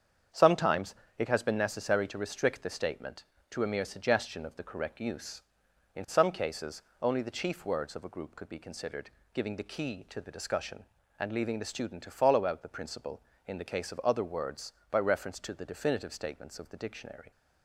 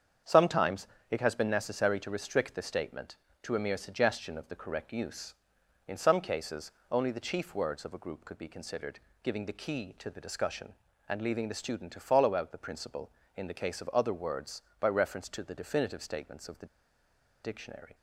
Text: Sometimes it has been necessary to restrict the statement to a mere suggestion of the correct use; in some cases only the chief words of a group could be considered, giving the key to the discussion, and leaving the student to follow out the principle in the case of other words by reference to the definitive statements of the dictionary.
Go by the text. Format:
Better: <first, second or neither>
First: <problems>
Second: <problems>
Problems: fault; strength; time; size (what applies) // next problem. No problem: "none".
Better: first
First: starts louder than the rest; strong; until 1.5 s; 7.5 dB // pauses between "Sometimes" and "it"; slight; at 0.9 s; 0.22 s long // pauses between "cases" and "only"; slight; at 6.8 s; 0.18 s long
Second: starts louder than the rest; strong; until 1.4 s; 7.5 dB // pauses between "Sometimes" and "it"; slight; at 0.8 s; 0.22 s long // pauses between "cases" and "only"; slight; at 6.7 s; 0.18 s long // pauses between "the" and "dictionary"; noticeable; at 16.6 s; 0.77 s long